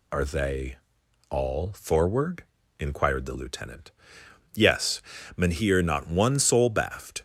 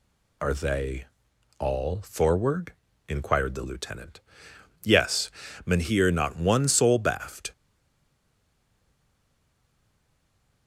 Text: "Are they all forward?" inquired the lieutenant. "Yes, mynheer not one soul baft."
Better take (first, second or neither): first